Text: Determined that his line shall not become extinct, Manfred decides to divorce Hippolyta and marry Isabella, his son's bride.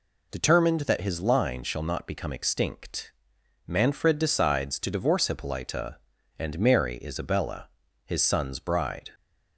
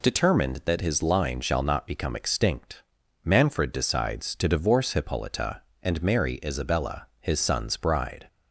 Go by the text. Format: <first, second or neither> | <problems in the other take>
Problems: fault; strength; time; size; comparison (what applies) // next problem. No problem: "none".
neither | none